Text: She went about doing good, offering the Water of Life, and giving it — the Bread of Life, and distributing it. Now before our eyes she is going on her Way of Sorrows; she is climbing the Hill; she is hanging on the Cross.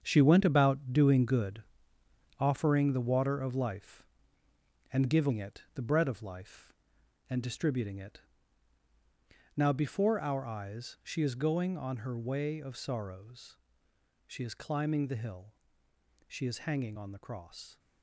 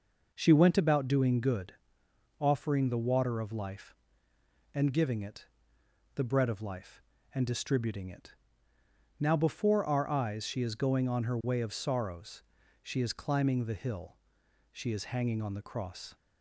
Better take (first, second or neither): second